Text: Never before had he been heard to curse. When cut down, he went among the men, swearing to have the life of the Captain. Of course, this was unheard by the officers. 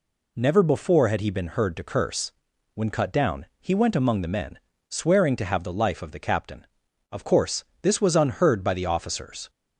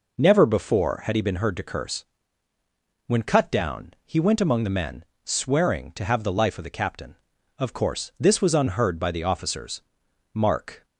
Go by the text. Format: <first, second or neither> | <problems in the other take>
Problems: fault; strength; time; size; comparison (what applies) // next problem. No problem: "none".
first | goes on to say "Mark"; from 10.3 s on; 0.52 s long